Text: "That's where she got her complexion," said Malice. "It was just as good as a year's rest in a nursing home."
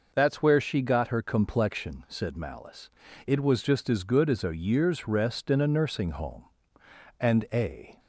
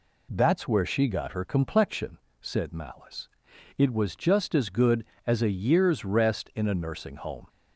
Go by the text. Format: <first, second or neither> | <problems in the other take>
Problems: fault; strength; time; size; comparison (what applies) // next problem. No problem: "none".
second | goes on to say "And a"; noticeable; from 7.2 s on; 0.78 s long